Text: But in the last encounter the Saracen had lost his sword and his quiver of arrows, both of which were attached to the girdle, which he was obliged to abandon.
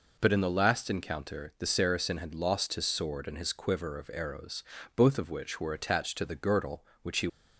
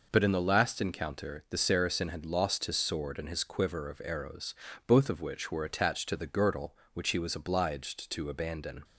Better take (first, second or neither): second